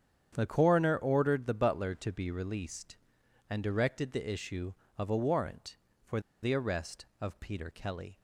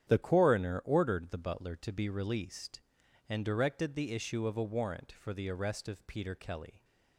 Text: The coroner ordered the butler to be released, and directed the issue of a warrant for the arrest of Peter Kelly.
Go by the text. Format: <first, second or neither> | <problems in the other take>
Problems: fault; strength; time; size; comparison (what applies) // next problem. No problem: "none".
second | starts louder than the rest; strong; until 1.3 s; 8.5 dB; strong in the second // pauses between "for" and "the"; slight; at 6.1 s; 0.23 s long